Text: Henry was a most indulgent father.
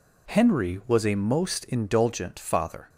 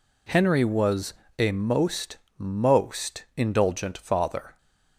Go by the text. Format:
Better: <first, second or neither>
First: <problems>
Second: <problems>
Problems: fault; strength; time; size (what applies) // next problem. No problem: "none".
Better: first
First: none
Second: pauses between "was" and "a"; slight; at 1.1 s; 0.26 s long // says "most" twice; at 2.3 s